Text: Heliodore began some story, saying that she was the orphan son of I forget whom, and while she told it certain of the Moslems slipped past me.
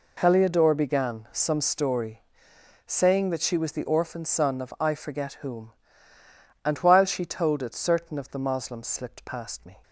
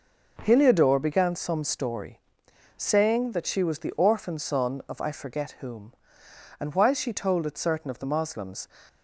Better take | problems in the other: first | stops before "slipped past me"; at 8.8 s

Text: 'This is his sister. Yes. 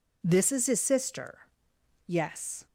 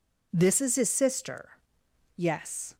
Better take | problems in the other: neither | none

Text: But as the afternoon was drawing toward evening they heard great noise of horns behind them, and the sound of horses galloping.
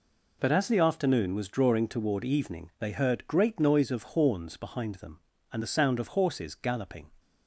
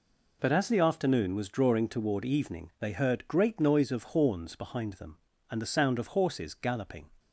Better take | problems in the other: neither | none

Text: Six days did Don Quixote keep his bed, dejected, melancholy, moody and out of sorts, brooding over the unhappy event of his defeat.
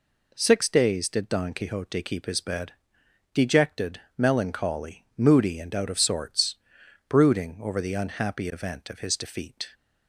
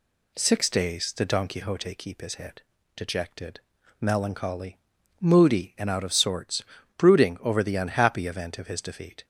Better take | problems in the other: first | says "head" for "bed"; at 2.3 s

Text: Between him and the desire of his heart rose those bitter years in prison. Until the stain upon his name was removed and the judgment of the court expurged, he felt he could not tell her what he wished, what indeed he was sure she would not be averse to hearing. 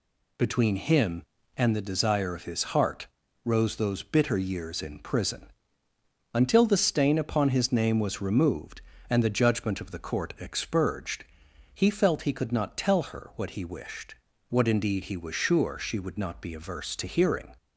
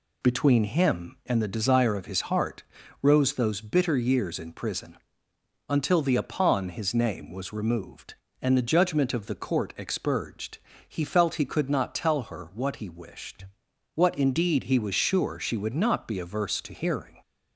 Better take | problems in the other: first | pauses between "heart" and "rose"; at 2.6 s; 0.40 s long; also in the first // skips "stain"; at 6.1 s

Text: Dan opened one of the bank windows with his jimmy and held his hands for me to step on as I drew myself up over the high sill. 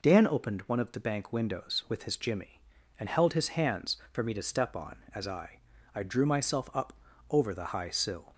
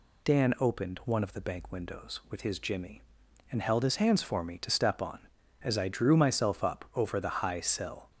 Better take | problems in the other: second | says "I" twice; at 5.9 s // pauses between "up" and "over"; at 6.9 s; 0.38 s long

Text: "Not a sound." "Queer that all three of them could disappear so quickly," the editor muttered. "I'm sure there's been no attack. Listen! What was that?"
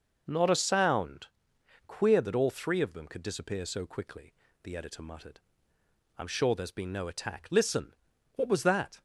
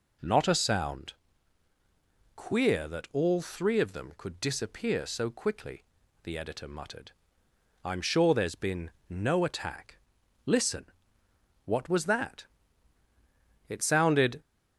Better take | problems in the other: first | pauses between "been" and "no"; slight; at 8.9 s; 0.20 s long // goes on to say "It sounded"; noticeable; from 13.6 s on; 0.72 s long

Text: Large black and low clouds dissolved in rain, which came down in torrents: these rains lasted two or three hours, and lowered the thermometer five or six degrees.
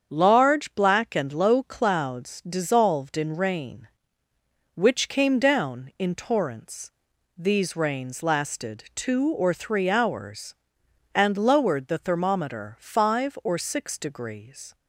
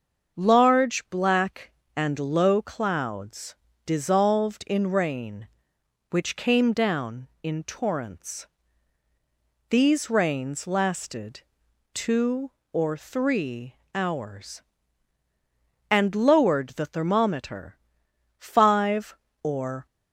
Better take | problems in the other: first | starts louder than the rest; until 1.4 s; 6.5 dB; strong in the first // pauses between "clouds" and "dissolved"; slight; at 3.5 s; 0.32 s long // pauses between "lasted" and "two"; noticeable; at 11.4 s; 0.52 s long // pauses between "three" and "hours"; slight; at 13.7 s; 0.18 s long // pauses between "thermometer" and "five"; noticeable; at 17.7 s; 0.62 s long // stops before "six degrees"; at 19.8 s

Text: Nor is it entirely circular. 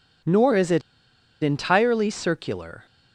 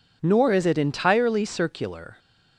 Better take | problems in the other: second | pauses between "it" and "entirely"; noticeable; at 0.8 s; 0.62 s long

